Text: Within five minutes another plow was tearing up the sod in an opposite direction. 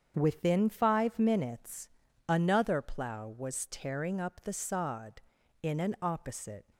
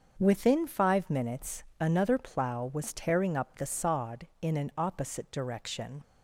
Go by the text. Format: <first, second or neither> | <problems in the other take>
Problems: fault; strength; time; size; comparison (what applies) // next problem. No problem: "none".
second | starts louder than the rest; strong; until 1.1 s; 7.5 dB; also in the second // pauses between "minutes" and "another"; at 1.8 s; 0.40 s long; slight in the second // stops before "direction"; at 6.7 s